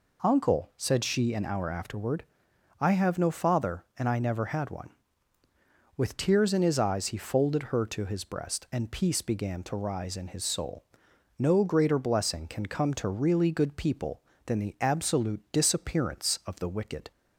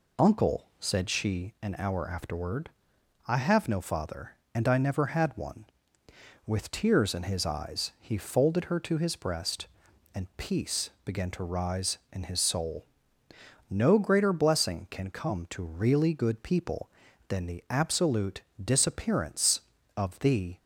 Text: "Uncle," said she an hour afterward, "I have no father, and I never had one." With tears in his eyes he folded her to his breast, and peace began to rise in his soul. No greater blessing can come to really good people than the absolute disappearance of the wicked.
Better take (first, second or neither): first